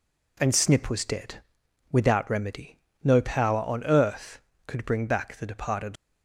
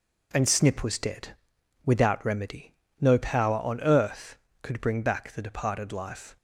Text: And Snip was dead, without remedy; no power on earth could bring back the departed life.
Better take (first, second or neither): second